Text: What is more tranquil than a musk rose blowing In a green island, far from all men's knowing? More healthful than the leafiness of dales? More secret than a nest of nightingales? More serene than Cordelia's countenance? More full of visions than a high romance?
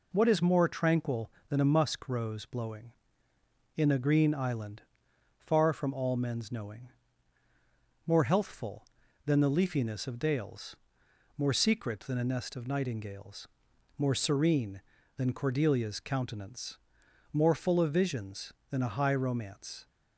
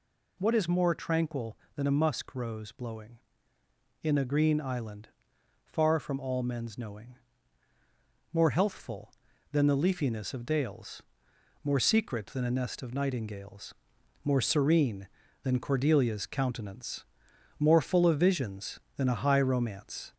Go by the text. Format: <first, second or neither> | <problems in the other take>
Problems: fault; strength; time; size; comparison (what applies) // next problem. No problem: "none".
first | gets louder; slight; throughout; 3 dB